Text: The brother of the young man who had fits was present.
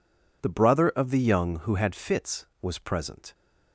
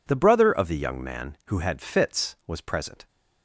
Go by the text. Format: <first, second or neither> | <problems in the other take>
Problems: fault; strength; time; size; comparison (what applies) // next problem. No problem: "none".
second | skips "man"; at 1.6 s